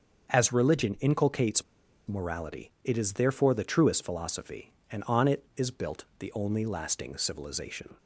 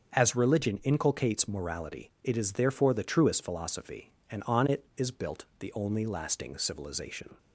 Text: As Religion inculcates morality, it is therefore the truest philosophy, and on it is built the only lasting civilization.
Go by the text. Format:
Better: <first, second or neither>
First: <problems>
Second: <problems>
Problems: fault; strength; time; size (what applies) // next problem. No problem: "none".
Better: second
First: starts louder than the rest; until 1.3 s; 6.5 dB // pauses between "inculcates" and "morality"; at 1.6 s; 0.43 s long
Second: starts louder than the rest; until 1.1 s; 6.5 dB